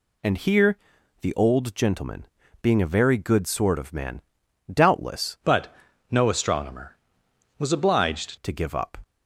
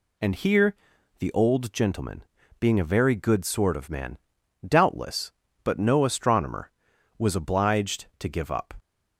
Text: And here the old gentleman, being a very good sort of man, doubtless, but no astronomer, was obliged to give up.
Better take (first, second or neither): second